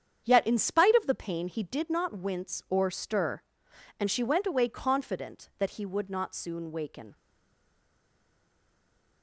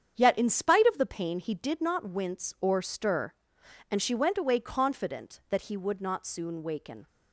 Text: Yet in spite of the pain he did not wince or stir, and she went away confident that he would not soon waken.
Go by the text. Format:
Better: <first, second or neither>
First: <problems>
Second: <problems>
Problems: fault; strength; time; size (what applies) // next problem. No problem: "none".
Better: second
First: starts louder than the rest; strong; until 1.2 s; 8 dB // stays silent after the last word; noticeable; from 7.1 s on; 2.1 s long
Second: starts louder than the rest; strong; until 1.1 s; 8 dB